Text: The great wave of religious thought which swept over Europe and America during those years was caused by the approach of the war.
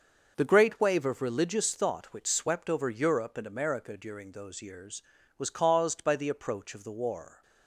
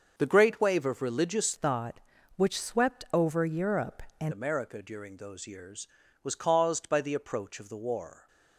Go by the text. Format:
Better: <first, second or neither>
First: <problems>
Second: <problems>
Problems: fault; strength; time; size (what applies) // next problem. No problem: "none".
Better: first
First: starts louder than the rest; noticeable; until 1.4 s; 6 dB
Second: starts louder than the rest; until 1.1 s; 6 dB // changes voice from "thought" to "and"; from 1.5 to 4.3 s; 2.8 s long